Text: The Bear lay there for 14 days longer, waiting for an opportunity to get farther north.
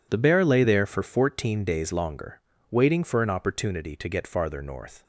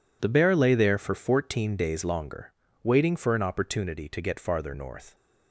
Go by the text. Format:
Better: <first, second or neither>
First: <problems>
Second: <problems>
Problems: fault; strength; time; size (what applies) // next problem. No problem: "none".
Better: neither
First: none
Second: none